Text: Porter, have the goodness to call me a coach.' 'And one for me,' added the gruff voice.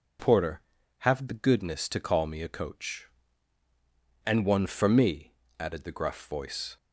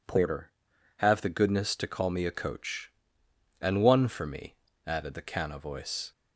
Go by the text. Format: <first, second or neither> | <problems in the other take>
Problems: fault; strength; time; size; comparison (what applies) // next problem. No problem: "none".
first | says "canna" for "gruff"; at 5.2 s